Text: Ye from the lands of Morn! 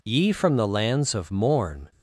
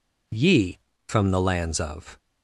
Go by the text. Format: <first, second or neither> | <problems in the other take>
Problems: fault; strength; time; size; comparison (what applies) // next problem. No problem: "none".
first | stops before "Morn"; at 2.1 s